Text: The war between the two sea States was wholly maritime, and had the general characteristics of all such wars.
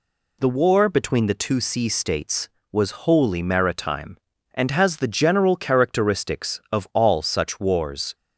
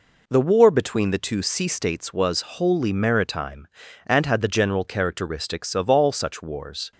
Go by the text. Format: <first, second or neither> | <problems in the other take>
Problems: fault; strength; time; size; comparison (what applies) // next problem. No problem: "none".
second | says "has" for "had"; at 4.7 s